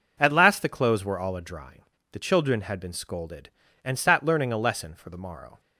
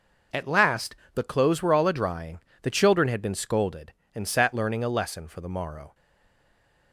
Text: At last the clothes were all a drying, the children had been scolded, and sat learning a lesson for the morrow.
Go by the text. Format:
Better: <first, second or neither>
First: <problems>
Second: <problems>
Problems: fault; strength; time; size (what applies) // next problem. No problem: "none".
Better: first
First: none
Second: pauses between "last" and "the"; slight; at 0.9 s; 0.20 s long // stays silent after the last word; from 5.9 s on; 1.0 s long